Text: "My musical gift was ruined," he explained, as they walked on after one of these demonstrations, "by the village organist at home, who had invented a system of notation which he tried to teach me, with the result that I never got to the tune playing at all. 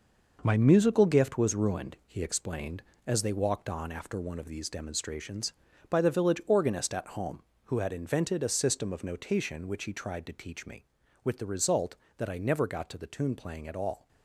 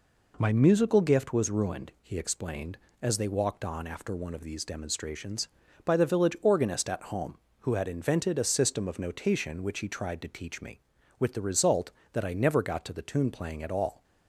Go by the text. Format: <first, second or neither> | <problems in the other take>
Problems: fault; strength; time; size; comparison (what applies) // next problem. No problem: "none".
second | gets quieter; strong; throughout; 7.5 dB